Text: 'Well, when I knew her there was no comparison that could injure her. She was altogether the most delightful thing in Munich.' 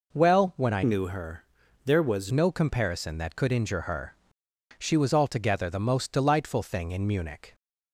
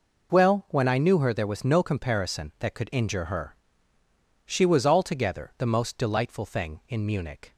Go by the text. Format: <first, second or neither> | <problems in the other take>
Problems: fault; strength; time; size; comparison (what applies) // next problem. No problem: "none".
second | changes voice from "knew" to "was"; from 0.8 to 2.3 s; 1.5 s long // pauses between "her" and "there"; at 1.4 s; 0.42 s long